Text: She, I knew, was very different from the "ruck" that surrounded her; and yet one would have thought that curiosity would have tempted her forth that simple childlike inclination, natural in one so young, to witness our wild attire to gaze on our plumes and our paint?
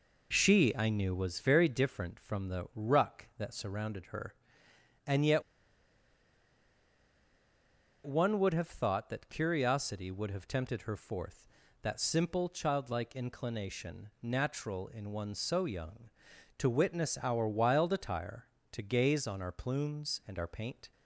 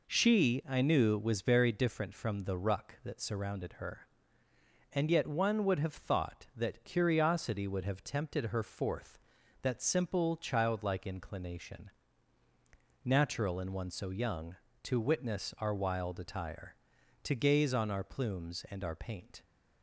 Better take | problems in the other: second | pauses between "yet" and "one"; strong; at 5.4 s; 2.6 s long

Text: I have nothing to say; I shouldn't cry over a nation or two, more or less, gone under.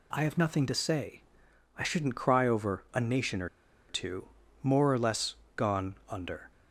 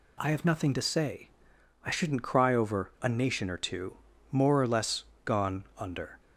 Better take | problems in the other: second | pauses between "or" and "two"; at 3.4 s; 0.41 s long

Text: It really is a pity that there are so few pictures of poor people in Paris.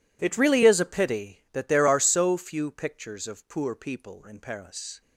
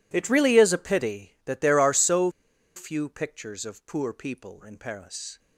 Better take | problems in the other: first | pauses between "so" and "few"; noticeable; at 2.2 s; 0.46 s long

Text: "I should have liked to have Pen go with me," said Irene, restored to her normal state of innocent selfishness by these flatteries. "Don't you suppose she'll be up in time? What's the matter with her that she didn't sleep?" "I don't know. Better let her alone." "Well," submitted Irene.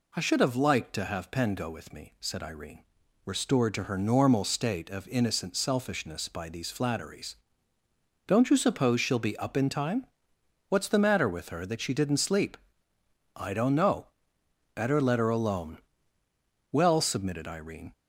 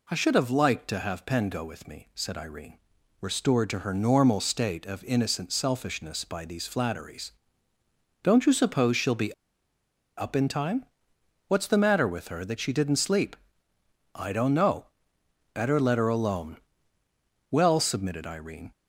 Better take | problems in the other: first | pauses between "be" and "up"; noticeable; at 9.3 s; 0.85 s long

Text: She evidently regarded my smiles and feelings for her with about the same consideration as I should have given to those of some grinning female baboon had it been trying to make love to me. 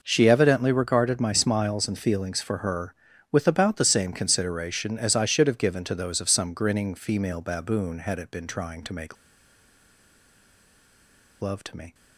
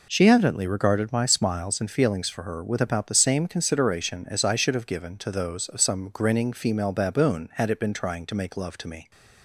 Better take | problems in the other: second | pauses between "make" and "love"; strong; at 9.1 s; 2.2 s long

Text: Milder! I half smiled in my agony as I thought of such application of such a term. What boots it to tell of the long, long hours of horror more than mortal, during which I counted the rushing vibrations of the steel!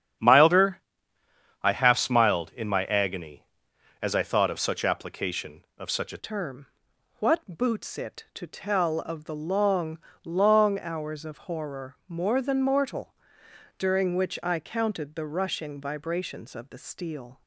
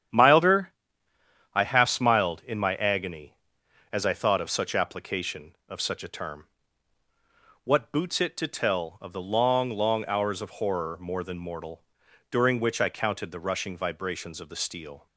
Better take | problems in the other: second | starts louder than the rest; strong; until 2.0 s; 9 dB; strong in the second // changes voice at "term"; from 6.1 s on; 11.3 s long

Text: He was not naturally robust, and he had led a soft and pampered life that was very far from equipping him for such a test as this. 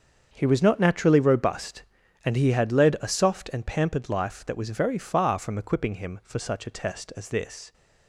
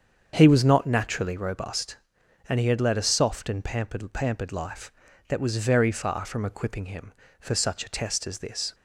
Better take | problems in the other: first | starts louder than the rest; strong; until 1.3 s; 7 dB; also in the first // says "pampered" twice; at 4.1 s

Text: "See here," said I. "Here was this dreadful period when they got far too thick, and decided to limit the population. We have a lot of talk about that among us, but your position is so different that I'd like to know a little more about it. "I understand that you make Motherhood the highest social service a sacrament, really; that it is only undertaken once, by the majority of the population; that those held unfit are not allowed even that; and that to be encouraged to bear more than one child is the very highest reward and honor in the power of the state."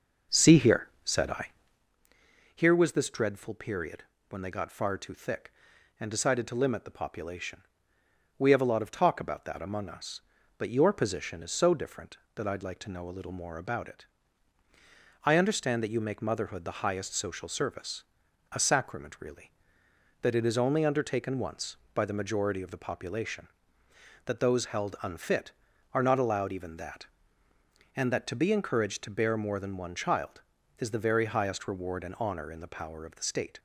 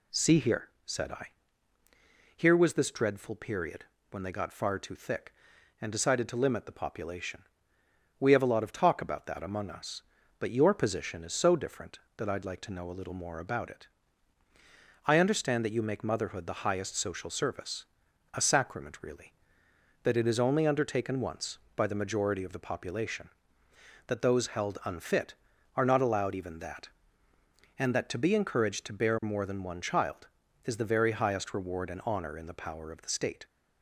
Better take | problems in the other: second | starts louder than the rest; noticeable; until 1.9 s; 6 dB // pauses between "period" and "when"; slight; at 4.0 s; 0.24 s long; slight in the second // pauses between "service" and "a"; noticeable; at 18.0 s; 0.48 s long; noticeable in the second

